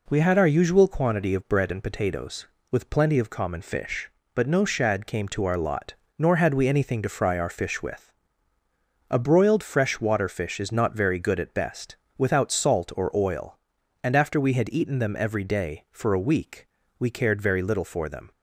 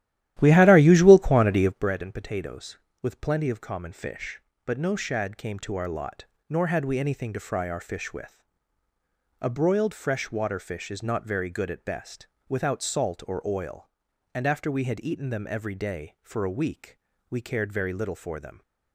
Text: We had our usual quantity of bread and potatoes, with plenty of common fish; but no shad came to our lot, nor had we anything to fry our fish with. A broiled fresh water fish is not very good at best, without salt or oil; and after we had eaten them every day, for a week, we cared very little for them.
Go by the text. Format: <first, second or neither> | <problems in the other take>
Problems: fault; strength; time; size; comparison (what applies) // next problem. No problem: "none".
first | starts louder than the rest; strong; until 1.9 s; 13 dB